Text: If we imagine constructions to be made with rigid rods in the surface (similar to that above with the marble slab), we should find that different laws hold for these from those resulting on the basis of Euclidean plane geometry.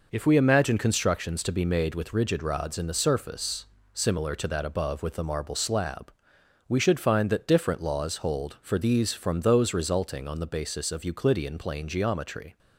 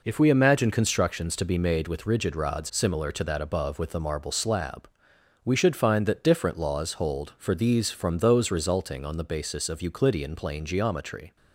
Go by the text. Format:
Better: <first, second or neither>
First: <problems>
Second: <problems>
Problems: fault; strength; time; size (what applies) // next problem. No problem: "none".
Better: first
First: none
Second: skips "in the surface"; at 2.6 s